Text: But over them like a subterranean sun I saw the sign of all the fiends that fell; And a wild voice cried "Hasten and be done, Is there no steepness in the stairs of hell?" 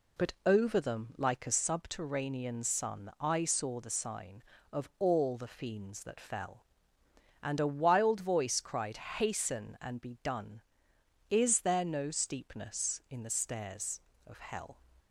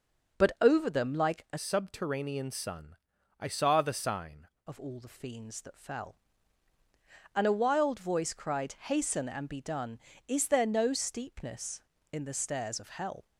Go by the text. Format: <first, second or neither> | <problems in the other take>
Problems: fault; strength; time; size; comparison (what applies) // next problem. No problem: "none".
first | changes voice from "subterranean" to "sign"; from 1.5 to 4.4 s; 2.9 s long // pauses between "sun" and "I"; at 2.9 s; 0.44 s long